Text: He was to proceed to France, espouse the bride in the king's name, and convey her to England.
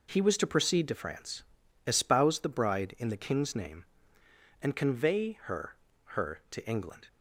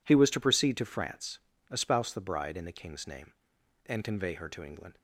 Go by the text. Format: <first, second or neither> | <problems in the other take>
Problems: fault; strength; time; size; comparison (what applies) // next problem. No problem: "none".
second | says "her" twice; at 6.1 s